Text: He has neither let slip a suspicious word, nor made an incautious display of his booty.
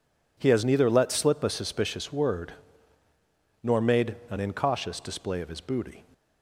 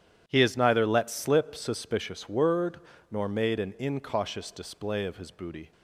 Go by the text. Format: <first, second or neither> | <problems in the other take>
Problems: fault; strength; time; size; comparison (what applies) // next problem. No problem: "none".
first | starts louder than the rest; strong; until 1.2 s; 10 dB // skips "a"; at 1.5 s